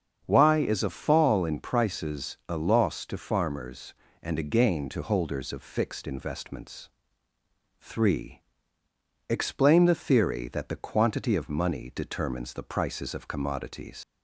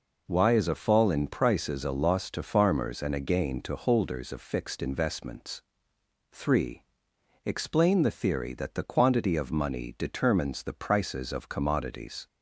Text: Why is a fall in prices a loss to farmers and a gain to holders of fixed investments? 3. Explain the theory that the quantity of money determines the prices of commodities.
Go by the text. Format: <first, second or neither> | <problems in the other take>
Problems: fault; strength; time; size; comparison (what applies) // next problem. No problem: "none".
second | starts louder than the rest; strong; until 1.2 s; 7 dB // leaves "commodities" unfinished; at 14.0 s; 100 ms